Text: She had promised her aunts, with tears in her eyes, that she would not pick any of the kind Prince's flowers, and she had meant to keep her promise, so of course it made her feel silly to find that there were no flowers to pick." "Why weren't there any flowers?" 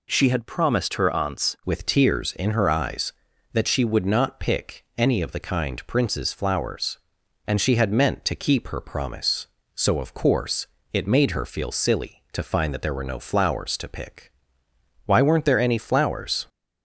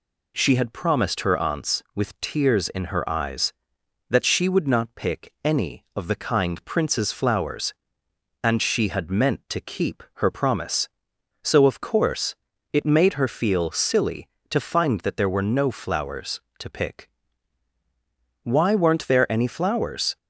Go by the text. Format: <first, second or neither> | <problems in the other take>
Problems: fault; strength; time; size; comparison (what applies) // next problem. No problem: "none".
second | changes voice at "with"; from 1.6 s on; 14.8 s long // pauses between "course" and "it"; slight; at 10.6 s; 0.28 s long; also in the second